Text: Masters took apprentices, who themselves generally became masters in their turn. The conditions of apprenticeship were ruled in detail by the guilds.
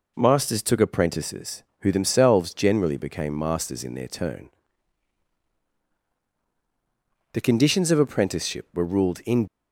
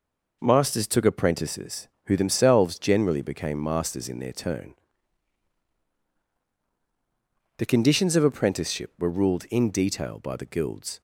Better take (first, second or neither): second